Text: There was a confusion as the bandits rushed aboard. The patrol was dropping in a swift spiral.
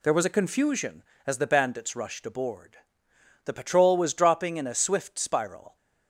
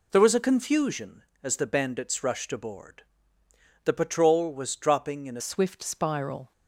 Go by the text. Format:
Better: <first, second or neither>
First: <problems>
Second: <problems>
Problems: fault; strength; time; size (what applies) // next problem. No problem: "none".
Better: first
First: none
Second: changes voice at "swift"; from 5.3 s on; 1.2 s long